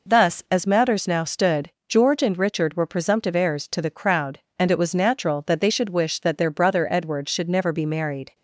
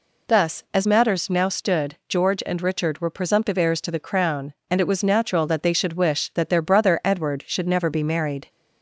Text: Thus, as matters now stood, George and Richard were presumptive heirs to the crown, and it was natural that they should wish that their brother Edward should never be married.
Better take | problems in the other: second | says "crowd" for "crown"; at 3.9 s

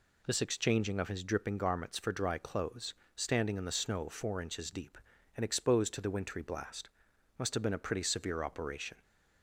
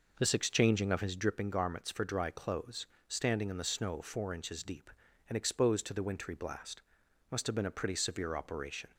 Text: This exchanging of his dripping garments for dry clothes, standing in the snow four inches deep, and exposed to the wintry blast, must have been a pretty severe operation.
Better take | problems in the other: first | starts louder than the rest; noticeable; until 1.4 s; 5.5 dB

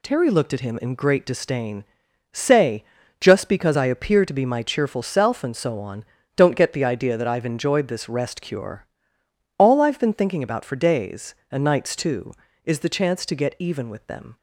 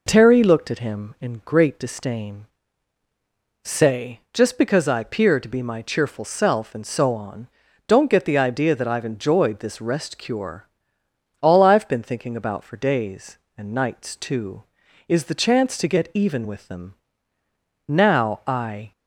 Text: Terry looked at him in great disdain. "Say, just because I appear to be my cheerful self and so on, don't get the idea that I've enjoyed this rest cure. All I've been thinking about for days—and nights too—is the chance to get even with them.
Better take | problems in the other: first | goes on to say "Now I"; noticeable; from 17.8 s on; 1.0 s long

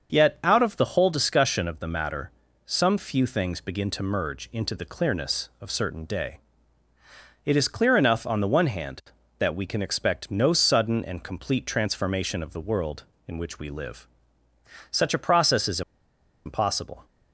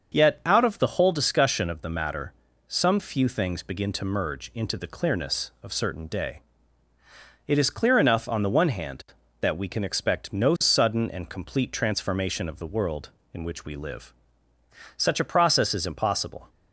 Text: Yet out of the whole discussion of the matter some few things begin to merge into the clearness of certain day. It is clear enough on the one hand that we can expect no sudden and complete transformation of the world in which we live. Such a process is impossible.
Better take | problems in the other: second | starts louder than the rest; until 1.1 s; 6.5 dB; also in the second // pauses between "matter" and "some"; at 2.2 s; 0.38 s long; also in the second // pauses between "is" and "impossible"; noticeable; at 15.8 s; 0.64 s long

